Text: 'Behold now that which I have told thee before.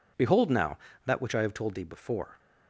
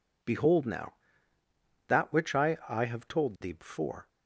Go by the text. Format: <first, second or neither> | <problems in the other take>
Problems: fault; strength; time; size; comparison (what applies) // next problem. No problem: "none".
first | says "I" twice; at 2.6 s